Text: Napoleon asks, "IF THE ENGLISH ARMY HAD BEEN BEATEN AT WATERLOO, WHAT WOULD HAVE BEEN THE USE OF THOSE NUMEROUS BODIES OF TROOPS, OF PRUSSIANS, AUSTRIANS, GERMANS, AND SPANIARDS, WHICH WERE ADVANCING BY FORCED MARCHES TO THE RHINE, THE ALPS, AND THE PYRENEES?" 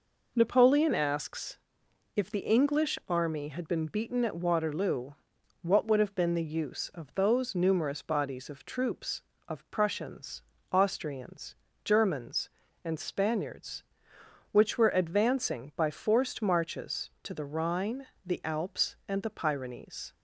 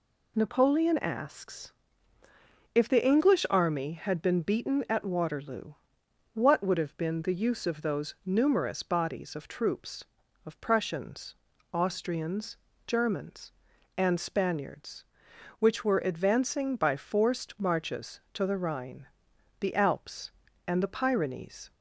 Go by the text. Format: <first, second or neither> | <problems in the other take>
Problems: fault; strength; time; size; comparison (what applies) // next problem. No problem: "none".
neither | none